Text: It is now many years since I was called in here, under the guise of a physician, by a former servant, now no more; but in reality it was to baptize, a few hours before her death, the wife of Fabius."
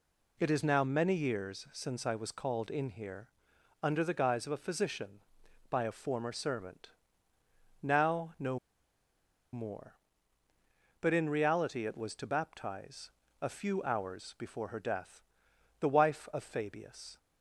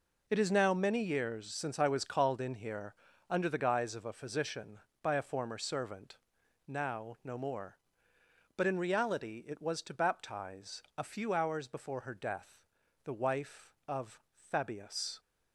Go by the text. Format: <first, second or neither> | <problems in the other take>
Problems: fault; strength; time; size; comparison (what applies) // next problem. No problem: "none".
second | pauses between "no" and "more"; noticeable; at 8.5 s; 0.94 s long